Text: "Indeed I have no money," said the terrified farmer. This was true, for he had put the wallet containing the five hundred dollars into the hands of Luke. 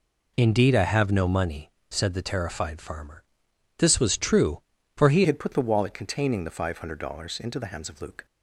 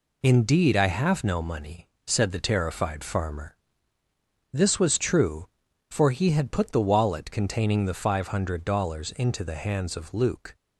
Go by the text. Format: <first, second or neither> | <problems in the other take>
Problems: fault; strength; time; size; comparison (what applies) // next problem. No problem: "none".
second | changes voice at "had"; from 5.2 s on; 3.0 s long